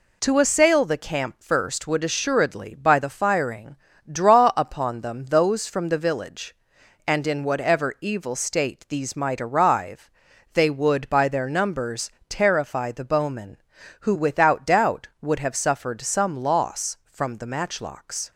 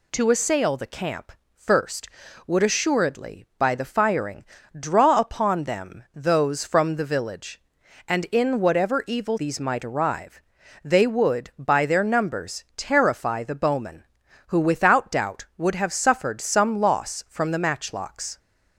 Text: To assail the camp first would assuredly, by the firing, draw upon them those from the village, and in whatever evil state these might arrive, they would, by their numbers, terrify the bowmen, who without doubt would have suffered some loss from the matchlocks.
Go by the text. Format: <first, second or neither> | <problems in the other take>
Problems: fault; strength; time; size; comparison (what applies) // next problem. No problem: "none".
first | pauses between "camp" and "first"; slight; at 1.3 s; 0.22 s long // skips "state"; at 9.3 s